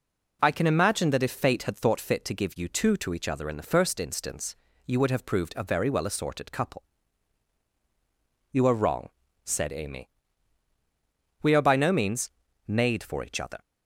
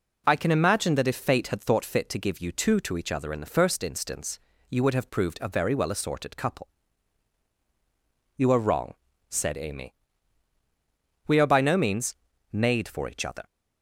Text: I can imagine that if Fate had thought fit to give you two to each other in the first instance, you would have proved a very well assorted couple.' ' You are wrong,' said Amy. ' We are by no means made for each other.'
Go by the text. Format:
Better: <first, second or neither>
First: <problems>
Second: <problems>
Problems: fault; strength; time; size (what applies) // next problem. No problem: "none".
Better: neither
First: starts louder than the rest; until 1.4 s; 6 dB // pauses between "means" and "made"; slight; at 12.3 s; 0.36 s long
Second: starts louder than the rest; until 1.2 s; 6 dB // pauses between "means" and "made"; slight; at 12.1 s; 0.36 s long